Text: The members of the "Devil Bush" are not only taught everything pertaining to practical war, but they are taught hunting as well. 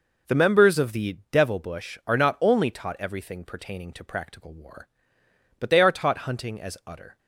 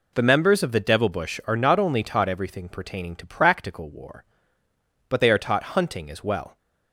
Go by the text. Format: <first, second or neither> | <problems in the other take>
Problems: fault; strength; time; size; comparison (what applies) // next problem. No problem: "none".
second | says "utter" for "well"; at 6.8 s